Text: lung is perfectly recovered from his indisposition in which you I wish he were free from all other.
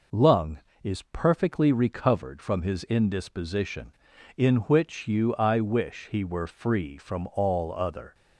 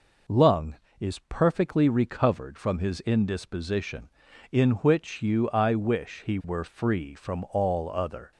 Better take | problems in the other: neither | none

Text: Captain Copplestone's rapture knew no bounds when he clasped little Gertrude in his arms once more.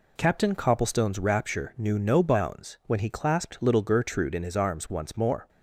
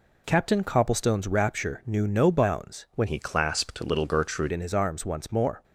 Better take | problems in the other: first | changes voice from "he" to "Gertrude"; from 3.0 to 4.5 s; 1.5 s long

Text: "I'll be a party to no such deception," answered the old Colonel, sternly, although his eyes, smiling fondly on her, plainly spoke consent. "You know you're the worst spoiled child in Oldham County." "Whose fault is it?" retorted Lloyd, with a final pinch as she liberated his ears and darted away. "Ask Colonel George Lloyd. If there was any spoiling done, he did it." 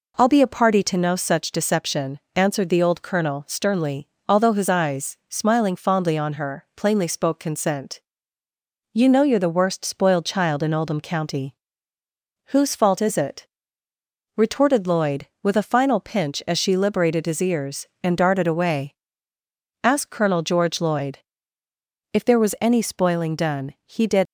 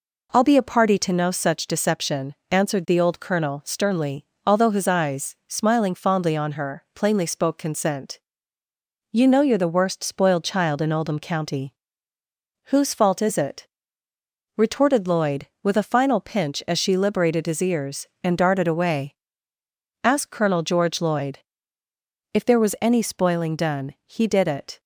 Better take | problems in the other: second | stops before "it"; at 24.2 s

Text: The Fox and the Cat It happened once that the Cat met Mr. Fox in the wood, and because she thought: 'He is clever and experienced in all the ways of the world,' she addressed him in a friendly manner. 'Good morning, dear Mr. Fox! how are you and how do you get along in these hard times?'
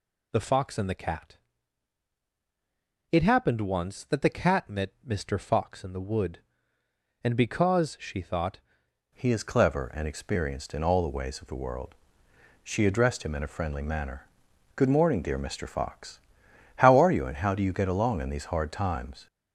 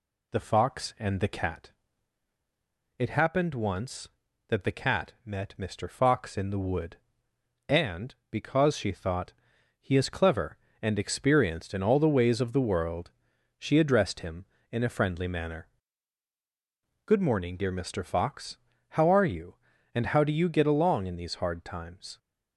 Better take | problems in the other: second | pauses between "Cat" and "It"; strong; at 1.3 s; 1.7 s long; strong in the second // changes voice at "He"; from 9.1 s on; 10.1 s long

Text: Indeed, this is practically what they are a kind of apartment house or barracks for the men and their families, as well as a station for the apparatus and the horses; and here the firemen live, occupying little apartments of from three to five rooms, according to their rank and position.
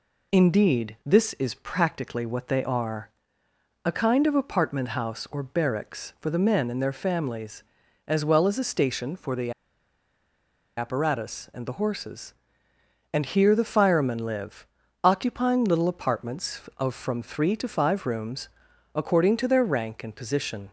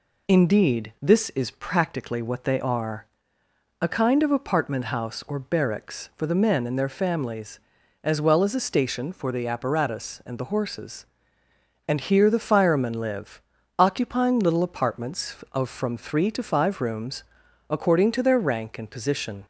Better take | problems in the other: second | pauses between "are" and "a"; noticeable; at 3.1 s; 0.74 s long; noticeable in the second // pauses between "the" and "apparatus"; strong; at 9.5 s; 1.2 s long

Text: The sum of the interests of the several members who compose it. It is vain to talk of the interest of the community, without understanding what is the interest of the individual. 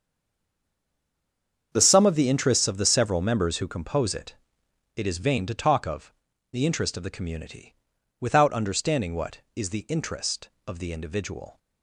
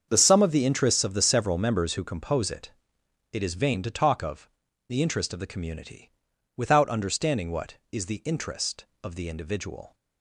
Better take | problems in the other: second | stays silent before the first word; noticeable; until 1.7 s; 1.7 s long // starts louder than the rest; strong; until 2.7 s; 7.5 dB; strong in the second // pauses between "of" and "the"; at 6.1 s; 0.40 s long; also in the second

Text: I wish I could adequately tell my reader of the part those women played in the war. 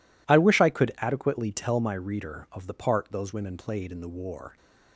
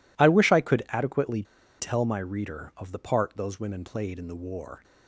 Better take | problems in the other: first | pauses between "adequately" and "tell"; at 1.4 s; 0.36 s long

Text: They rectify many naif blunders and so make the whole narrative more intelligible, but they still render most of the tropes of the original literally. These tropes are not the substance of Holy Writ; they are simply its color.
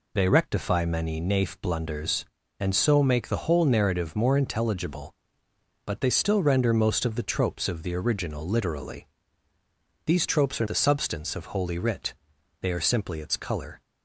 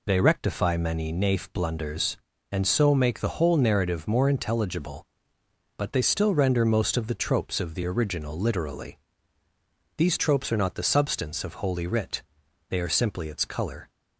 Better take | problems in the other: second | skips "not"; at 10.6 s

